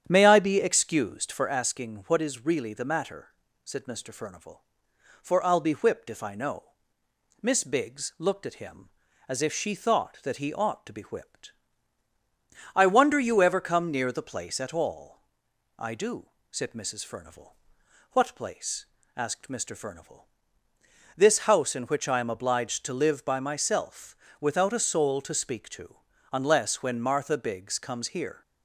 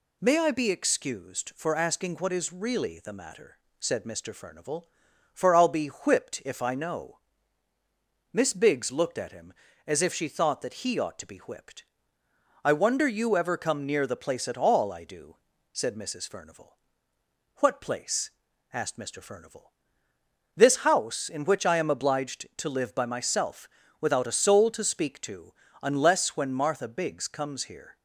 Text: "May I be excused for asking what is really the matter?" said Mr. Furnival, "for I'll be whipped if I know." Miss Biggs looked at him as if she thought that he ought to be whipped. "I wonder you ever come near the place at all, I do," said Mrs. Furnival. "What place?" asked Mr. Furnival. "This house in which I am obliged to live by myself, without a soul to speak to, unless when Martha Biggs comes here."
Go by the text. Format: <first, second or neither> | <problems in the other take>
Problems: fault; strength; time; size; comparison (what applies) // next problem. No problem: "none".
second | starts louder than the rest; strong; until 1.7 s; 9 dB